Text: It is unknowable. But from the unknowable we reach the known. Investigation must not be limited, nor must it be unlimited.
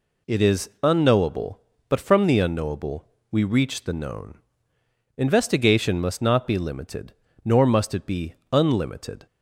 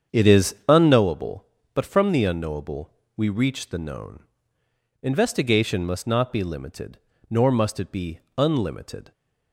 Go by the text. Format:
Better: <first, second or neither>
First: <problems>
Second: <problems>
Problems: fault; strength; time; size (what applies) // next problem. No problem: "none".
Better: first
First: pauses between "unknowable" and "we"; slight; at 3.0 s; 0.24 s long // pauses between "be" and "unlimited"; slight; at 8.3 s; 0.18 s long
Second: starts louder than the rest; strong; until 1.0 s; 8 dB // pauses between "unknowable" and "we"; slight; at 2.9 s; 0.24 s long // pauses between "be" and "unlimited"; slight; at 8.1 s; 0.18 s long